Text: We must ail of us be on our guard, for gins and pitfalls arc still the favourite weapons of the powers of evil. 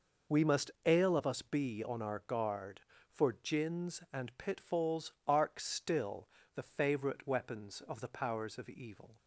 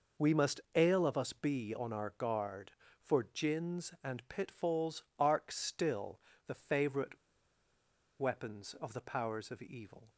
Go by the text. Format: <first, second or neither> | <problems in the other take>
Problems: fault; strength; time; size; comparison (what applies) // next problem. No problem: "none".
first | pauses between "still" and "the"; slight; at 6.1 s; 0.26 s long; slight in the first // pauses between "favourite" and "weapons"; at 7.1 s; 1.0 s long